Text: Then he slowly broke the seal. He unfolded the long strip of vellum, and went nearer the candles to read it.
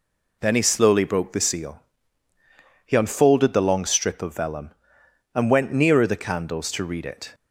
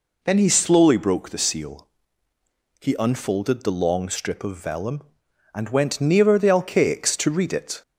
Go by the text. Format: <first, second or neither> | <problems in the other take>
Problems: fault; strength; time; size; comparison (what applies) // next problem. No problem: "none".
first | says "alcaics" for "candles"; at 6.4 s